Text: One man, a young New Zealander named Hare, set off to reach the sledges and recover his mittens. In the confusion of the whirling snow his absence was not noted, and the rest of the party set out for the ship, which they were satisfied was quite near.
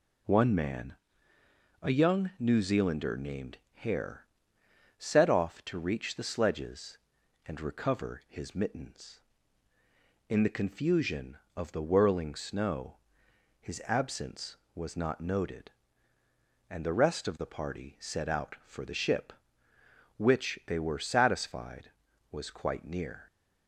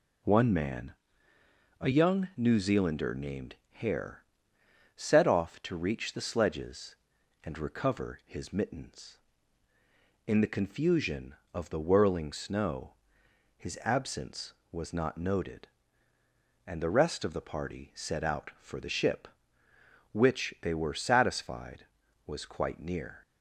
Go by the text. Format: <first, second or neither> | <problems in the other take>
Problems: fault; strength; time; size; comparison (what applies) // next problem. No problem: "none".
neither | pauses between "named" and "Hare"; slight; the same in both // pauses between "snow" and "his"; noticeable; the same in both